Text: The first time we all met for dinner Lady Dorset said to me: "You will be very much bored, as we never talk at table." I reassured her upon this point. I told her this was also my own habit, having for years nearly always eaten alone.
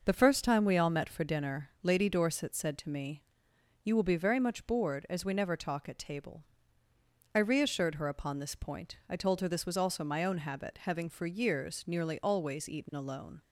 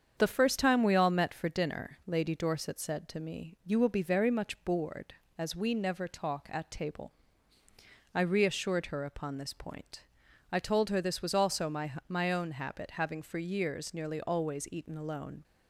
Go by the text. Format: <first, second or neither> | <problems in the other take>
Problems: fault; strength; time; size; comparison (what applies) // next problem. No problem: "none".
first | starts louder than the rest; strong; until 1.1 s; 7.5 dB // says "my" twice; at 12.0 s